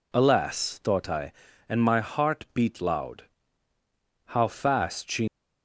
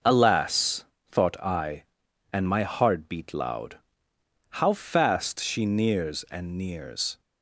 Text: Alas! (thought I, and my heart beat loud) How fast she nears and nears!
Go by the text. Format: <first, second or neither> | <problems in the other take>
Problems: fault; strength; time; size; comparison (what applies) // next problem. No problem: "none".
second | stops before "nears and nears"; at 5.2 s